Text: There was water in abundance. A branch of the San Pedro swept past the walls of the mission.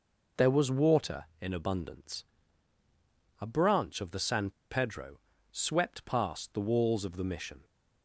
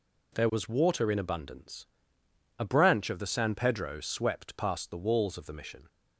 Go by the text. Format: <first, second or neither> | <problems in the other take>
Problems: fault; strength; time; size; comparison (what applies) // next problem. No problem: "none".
second | pauses between "San" and "Pedro"; slight; at 4.5 s; 0.20 s long // pauses between "Pedro" and "swept"; slight; at 5.1 s; 0.32 s long